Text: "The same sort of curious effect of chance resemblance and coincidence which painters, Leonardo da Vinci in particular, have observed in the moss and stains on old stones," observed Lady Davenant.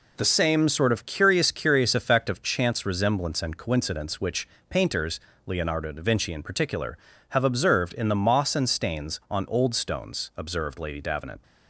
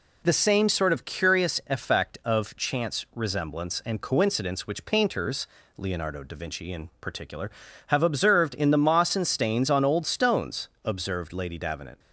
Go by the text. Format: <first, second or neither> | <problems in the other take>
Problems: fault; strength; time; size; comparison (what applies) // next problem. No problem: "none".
second | says "curious" twice; at 1.5 s // pauses between "which" and "painters"; slight; at 4.4 s; 0.22 s long